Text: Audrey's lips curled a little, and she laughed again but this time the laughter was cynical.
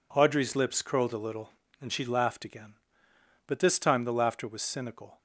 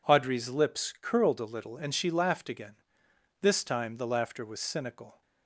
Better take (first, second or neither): first